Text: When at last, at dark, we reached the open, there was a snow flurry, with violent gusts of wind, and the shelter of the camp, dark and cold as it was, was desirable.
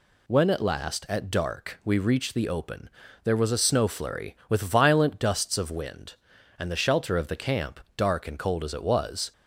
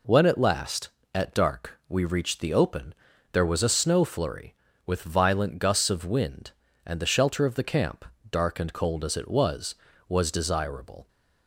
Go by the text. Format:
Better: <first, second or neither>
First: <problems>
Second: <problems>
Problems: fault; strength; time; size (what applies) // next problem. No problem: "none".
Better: second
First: stops before "was desirable"; at 9.3 s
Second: none